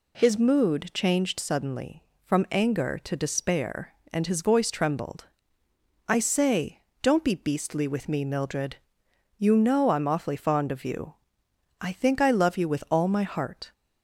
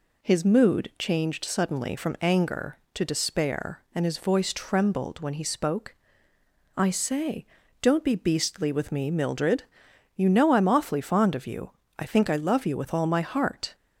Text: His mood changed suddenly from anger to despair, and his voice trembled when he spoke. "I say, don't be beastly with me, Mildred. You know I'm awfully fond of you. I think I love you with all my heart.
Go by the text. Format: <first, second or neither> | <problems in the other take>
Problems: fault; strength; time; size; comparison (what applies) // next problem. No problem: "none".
second | skips "when he spoke"; at 5.6 s